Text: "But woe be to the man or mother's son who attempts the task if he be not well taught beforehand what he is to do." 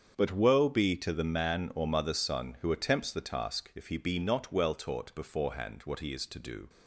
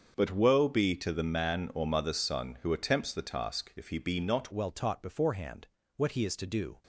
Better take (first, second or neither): first